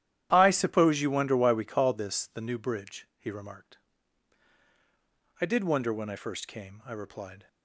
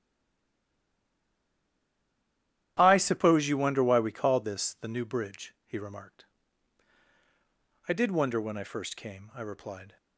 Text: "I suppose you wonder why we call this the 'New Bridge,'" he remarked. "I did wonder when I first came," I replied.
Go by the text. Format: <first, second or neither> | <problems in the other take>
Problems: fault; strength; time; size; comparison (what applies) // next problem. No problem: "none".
first | stays silent before the first word; strong; until 2.7 s; 2.7 s long // starts louder than the rest; strong; until 3.7 s; 11.5 dB; strong in the first